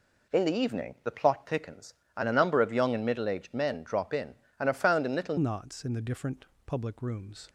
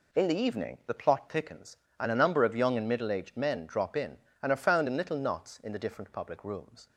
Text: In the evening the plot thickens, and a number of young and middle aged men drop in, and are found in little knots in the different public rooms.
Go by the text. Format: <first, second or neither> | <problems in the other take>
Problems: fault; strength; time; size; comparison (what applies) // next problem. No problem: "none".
second | changes voice at "knots"; from 5.3 s on; 2.1 s long // pauses between "different" and "public"; slight; at 6.4 s; 0.22 s long